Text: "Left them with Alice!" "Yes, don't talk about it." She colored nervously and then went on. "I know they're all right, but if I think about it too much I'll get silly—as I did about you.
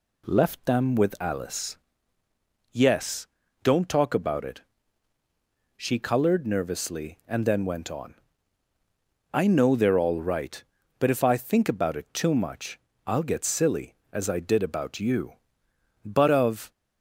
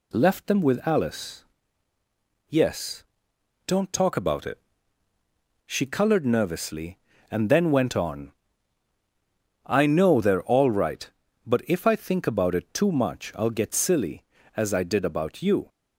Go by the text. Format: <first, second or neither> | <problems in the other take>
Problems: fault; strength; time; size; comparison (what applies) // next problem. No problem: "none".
second | pauses between "much" and "I'll"; slight; at 12.7 s; 0.26 s long // goes on to say "But of"; noticeable; from 16.0 s on; 0.66 s long